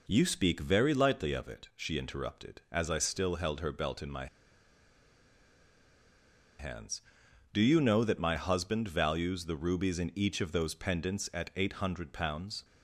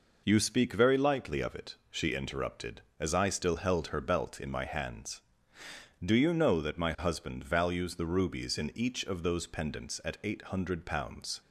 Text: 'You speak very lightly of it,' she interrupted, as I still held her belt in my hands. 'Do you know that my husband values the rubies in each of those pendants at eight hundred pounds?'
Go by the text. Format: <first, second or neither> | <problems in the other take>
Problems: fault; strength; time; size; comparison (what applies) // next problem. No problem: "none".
second | pauses between "my" and "hands"; strong; at 4.2 s; 2.3 s long